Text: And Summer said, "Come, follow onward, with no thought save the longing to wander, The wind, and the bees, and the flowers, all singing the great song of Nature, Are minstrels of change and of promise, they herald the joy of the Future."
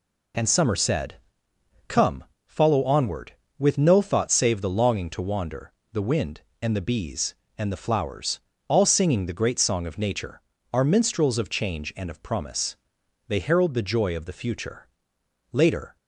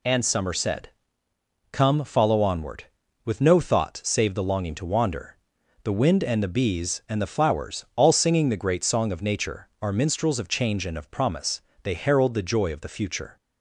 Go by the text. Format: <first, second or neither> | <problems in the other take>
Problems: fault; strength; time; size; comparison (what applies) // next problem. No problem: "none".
second | goes on to say "Later"; slight; from 15.5 s on; 0.42 s long